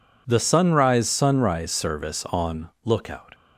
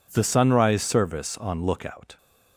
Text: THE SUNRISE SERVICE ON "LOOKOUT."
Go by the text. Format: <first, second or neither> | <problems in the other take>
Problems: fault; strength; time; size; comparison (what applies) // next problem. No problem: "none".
second | says "SUNRISE" twice; at 1.0 s // pauses between "ON" and "LOOKOUT"; slight; at 2.7 s; 0.16 s long